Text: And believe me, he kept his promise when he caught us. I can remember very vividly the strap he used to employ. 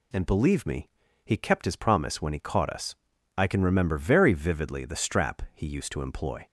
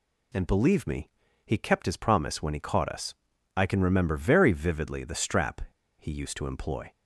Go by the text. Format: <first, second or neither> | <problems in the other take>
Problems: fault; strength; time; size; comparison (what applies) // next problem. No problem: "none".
first | pauses between "strap" and "he"; at 5.6 s; 0.37 s long